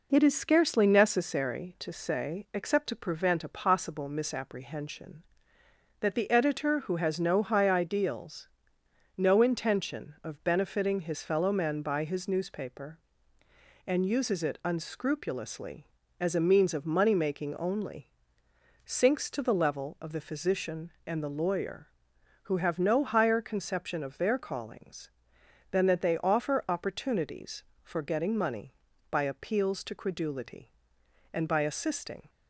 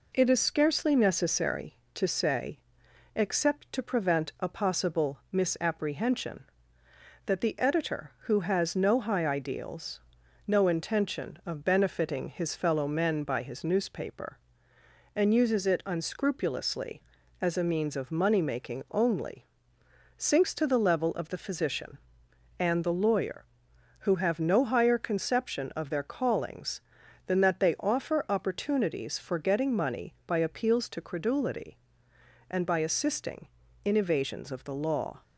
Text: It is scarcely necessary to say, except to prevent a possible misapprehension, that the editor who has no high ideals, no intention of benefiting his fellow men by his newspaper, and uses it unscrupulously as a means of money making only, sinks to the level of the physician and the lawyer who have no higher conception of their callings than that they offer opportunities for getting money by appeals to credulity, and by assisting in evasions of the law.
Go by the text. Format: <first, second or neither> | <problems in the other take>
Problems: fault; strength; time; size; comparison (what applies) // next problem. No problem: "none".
second | stops before "in evasions of the law"; at 32.2 s